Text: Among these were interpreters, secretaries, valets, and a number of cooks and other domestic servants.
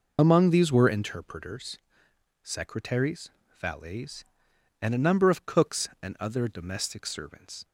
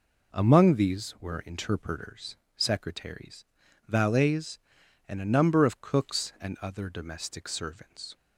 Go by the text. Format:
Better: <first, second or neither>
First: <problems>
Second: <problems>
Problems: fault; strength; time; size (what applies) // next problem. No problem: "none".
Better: second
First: loses the start of "Among"; at 0.1 s; 40 ms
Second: none